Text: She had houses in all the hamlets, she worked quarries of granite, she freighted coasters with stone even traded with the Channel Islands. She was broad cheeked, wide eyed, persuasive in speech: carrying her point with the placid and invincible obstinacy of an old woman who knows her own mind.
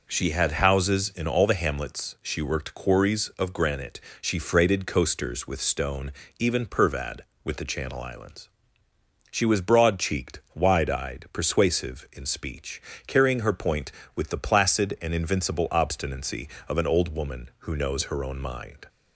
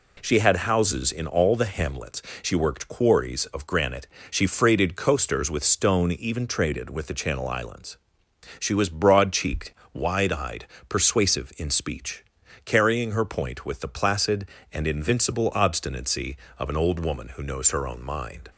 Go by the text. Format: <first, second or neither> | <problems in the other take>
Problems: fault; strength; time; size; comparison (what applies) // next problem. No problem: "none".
second | pauses between "stone" and "even"; slight; at 6.1 s; 0.26 s long // says "pervad" for "traded"; at 6.6 s